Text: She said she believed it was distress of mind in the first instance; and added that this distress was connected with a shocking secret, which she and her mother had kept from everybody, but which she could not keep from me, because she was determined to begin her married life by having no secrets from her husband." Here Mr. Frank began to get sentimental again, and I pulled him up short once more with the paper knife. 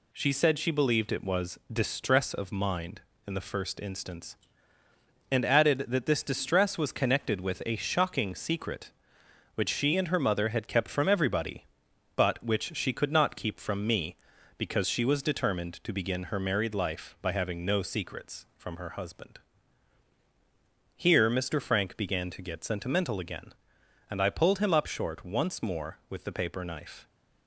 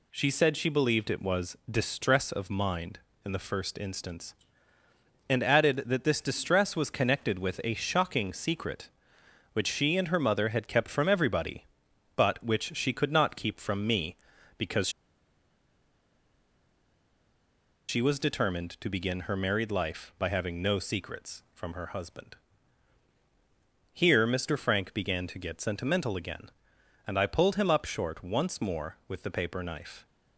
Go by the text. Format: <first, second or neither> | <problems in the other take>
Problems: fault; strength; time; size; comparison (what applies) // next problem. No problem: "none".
first | pauses between "because" and "she"; strong; at 14.8 s; 2.9 s long